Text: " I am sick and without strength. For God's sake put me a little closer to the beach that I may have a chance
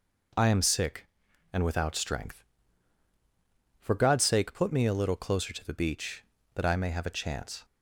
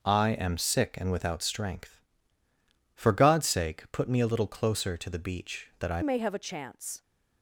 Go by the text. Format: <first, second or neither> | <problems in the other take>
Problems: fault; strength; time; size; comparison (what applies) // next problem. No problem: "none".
first | changes voice at "may"; from 6.0 s on; 1.0 s long